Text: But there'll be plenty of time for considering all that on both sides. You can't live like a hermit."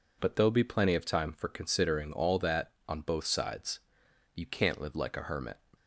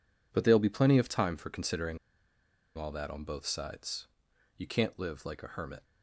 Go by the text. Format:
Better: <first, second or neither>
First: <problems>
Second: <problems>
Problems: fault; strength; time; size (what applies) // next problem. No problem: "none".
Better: first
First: none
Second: pauses between "considering" and "all"; noticeable; at 1.9 s; 0.79 s long